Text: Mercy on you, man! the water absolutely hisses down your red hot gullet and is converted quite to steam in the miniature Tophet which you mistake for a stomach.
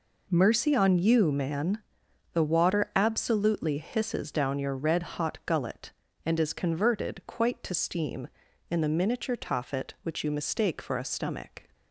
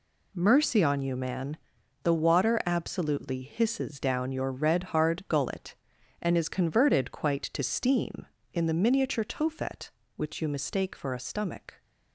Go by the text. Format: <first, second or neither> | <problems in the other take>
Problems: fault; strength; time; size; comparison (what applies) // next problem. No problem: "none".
first | says "hard" for "hot"; at 4.8 s